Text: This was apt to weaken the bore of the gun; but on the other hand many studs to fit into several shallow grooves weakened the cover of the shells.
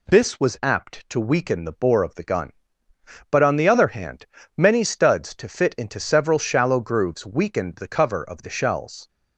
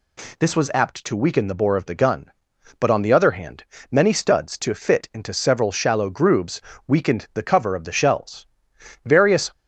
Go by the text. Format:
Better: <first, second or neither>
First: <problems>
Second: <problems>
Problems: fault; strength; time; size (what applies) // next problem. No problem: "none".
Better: first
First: pauses between "hand" and "many"; slight; at 4.2 s; 0.32 s long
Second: pauses between "hand" and "many"; slight; at 3.6 s; 0.26 s long // pauses between "grooves" and "weakened"; slight; at 6.6 s; 0.28 s long // goes on to say "Various"; slight; from 9.0 s on; 0.48 s long